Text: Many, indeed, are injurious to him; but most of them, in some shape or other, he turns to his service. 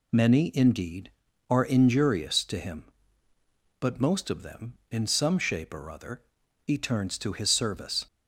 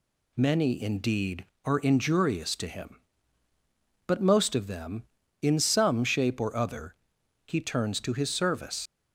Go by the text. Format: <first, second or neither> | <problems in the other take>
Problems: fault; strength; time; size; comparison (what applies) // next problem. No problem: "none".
first | leaves "service" unfinished; at 8.8 s; 95 ms